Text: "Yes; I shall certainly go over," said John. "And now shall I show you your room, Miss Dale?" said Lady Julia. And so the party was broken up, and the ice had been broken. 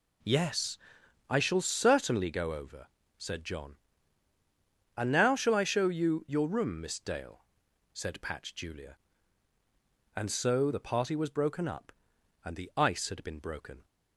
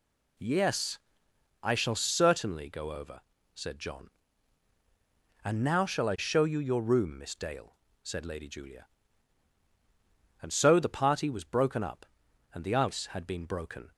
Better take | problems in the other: second | says "Patch" for "Lady"; at 8.2 s

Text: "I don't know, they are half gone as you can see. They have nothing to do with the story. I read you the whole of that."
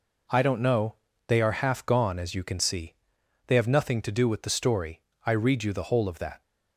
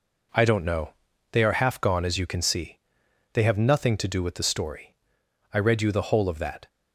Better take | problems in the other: neither | none

